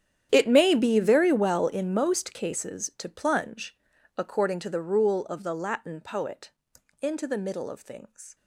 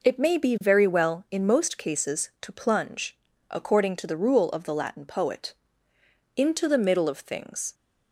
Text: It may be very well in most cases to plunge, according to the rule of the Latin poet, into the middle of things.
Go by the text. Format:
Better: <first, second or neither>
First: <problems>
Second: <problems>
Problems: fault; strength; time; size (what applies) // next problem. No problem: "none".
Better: second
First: gets quieter; strong; throughout; 19 dB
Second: none